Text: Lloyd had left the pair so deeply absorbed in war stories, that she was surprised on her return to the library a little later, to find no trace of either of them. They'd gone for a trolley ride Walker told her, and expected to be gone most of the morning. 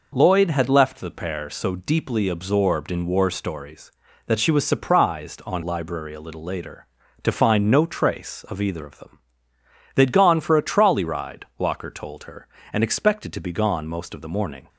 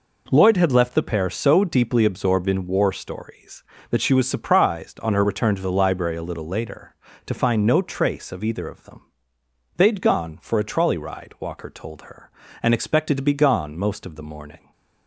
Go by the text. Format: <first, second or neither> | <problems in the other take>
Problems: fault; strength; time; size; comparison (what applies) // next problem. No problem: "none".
second | skips "her return to the"; at 5.6 s